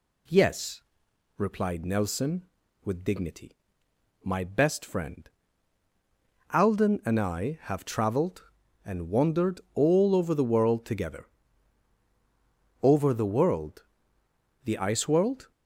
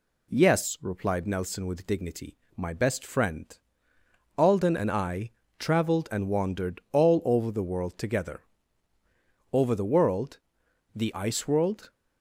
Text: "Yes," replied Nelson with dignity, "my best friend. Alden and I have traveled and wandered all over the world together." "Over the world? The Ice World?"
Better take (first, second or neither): first